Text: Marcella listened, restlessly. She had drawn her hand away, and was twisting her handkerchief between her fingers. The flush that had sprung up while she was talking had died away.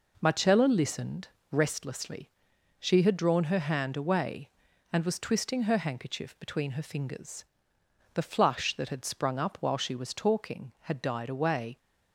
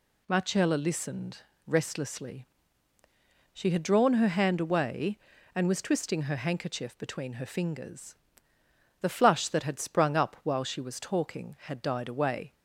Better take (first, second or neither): neither